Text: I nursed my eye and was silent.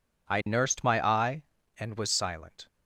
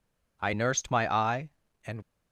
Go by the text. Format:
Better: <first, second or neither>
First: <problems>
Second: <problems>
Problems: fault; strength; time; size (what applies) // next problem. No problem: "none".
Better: first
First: none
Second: stops before "was silent"; at 2.0 s